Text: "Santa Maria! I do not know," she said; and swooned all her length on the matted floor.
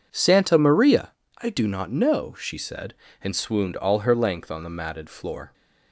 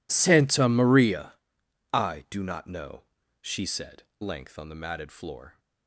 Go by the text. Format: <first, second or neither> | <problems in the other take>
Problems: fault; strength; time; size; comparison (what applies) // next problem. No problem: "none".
first | skips "and swooned all her"; at 4.1 s